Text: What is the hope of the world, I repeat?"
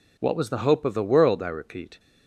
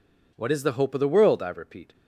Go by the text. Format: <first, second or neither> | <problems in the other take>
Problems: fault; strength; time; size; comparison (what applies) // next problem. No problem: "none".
second | says "was" for "is"; at 0.3 s